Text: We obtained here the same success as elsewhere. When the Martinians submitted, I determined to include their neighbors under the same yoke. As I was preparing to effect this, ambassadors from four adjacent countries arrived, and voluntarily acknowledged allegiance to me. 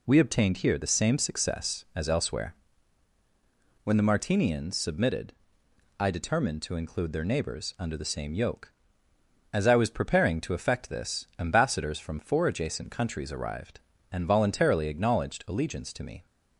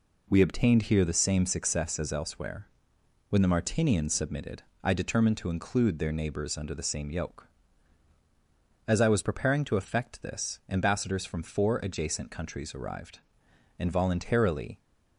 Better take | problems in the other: first | stops before "acknowledged allegiance to me"; at 14.7 s

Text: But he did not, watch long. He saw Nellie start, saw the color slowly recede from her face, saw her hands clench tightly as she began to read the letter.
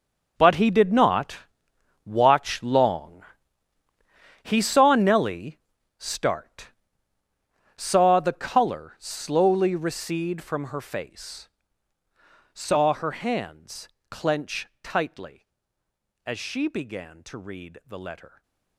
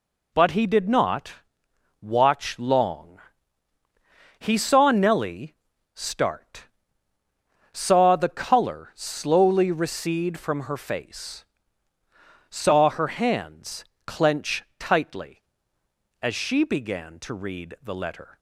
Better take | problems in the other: second | gets quieter; strong; throughout; 15 dB // pauses between "Nellie" and "start"; at 5.5 s; 0.40 s long; also in the second // pauses between "hands" and "clench"; slight; at 13.8 s; 0.22 s long; slight in the second // stays silent after the last word; slight; from 18.2 s on; 0.5 s long

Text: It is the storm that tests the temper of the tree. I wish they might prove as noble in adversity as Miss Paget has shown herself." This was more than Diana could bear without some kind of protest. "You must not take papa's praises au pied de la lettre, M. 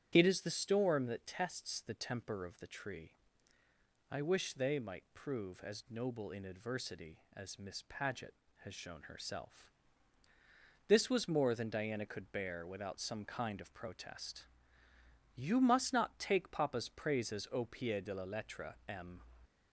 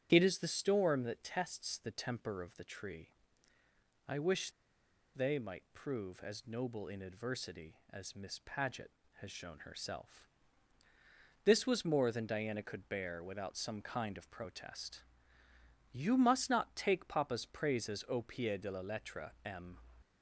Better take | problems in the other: first | starts louder than the rest; strong; until 1.1 s; 7.5 dB; strong in the first // pauses between "wish" and "they"; noticeable; at 4.5 s; 0.63 s long

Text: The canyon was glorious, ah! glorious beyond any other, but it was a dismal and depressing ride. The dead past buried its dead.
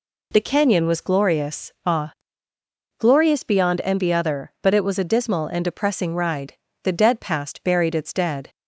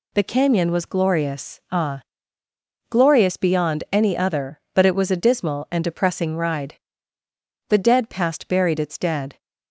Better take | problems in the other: second | says "envy" for "any"; at 3.8 s

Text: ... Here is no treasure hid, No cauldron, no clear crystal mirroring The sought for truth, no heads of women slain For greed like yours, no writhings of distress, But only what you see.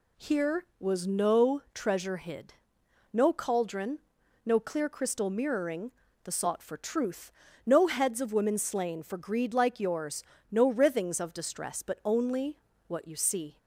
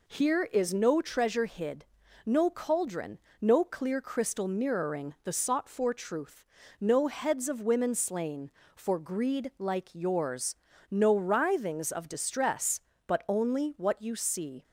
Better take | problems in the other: second | says "was" for "is"; at 0.7 s // pauses between "mirroring" and "The"; slight; at 5.9 s; 0.32 s long // pauses between "only" and "what"; slight; at 12.5 s; 0.28 s long

